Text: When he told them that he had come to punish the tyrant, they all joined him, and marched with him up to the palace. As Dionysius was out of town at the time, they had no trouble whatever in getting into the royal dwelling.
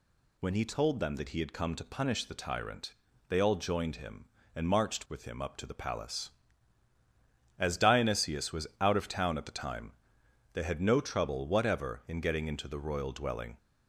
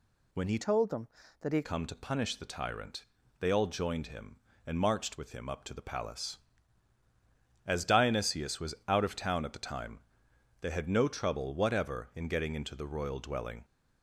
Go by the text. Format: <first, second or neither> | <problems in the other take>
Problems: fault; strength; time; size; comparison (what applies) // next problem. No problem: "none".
first | changes voice from "told" to "had"; from 0.6 to 1.6 s; 1.0 s long